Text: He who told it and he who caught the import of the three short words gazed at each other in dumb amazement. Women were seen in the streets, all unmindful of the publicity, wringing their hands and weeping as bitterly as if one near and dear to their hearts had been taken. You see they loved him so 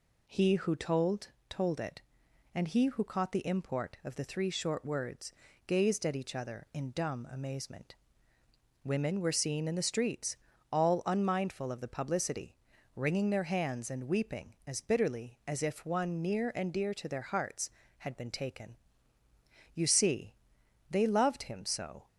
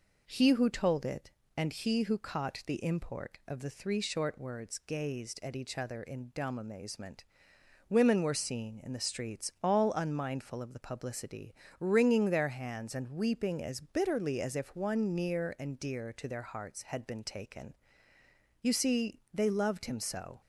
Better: second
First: says "told" twice; at 1.4 s // pauses between "words" and "gazed"; slight; at 5.3 s; 0.34 s long // pauses between "see" and "they"; noticeable; at 20.3 s; 0.56 s long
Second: none

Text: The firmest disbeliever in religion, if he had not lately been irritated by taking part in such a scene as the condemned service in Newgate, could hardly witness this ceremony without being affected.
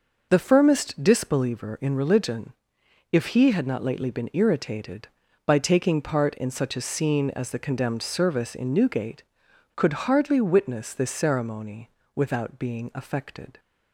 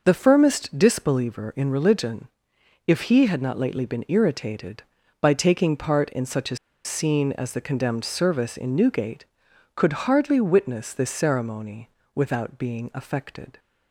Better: first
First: pauses between "ceremony" and "without"; slight; at 11.8 s; 0.26 s long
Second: pauses between "a" and "scene"; slight; at 6.5 s; 0.29 s long // pauses between "ceremony" and "without"; slight; at 11.8 s; 0.26 s long

